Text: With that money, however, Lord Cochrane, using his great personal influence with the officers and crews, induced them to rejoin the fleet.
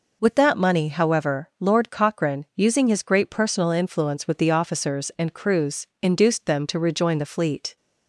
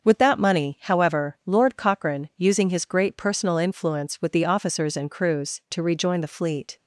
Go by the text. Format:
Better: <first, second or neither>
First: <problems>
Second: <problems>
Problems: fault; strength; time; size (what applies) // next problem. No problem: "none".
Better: first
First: none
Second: starts louder than the rest; until 1.0 s; 6.5 dB // skips "induced them"; at 5.6 s